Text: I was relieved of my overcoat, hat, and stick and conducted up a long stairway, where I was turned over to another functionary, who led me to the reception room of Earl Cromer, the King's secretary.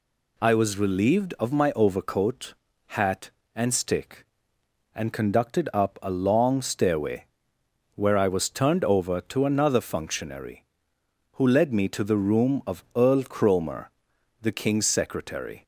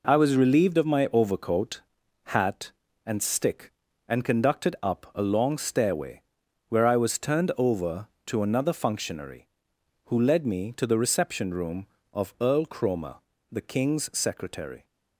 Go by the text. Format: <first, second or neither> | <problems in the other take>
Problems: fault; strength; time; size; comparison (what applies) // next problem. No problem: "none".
second | skips "reception"; at 12.1 s